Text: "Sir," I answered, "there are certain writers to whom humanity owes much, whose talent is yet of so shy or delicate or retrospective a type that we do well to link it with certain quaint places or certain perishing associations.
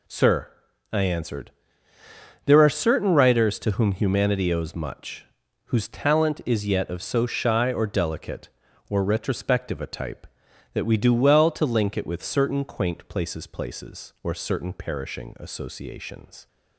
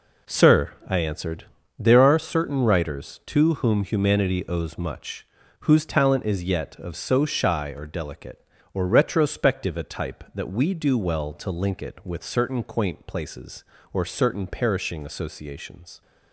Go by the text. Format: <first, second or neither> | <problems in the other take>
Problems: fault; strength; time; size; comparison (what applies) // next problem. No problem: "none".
second | says "places" twice; at 13.4 s